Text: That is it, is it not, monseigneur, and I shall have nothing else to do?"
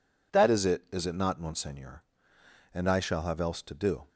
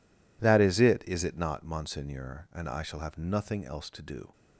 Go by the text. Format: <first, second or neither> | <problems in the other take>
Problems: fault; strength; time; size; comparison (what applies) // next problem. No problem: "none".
second | skips "nothing"; at 3.3 s